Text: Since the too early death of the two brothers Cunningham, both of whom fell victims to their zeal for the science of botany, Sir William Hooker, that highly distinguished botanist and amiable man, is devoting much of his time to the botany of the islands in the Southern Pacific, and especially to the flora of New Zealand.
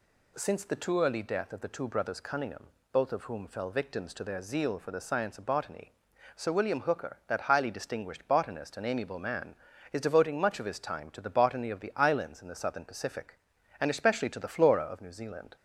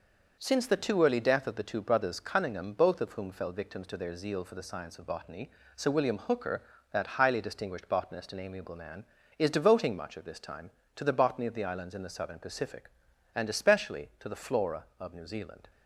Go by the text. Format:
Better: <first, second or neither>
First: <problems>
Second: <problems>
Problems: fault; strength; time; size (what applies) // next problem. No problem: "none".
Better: first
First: none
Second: says "this" for "his"; at 10.2 s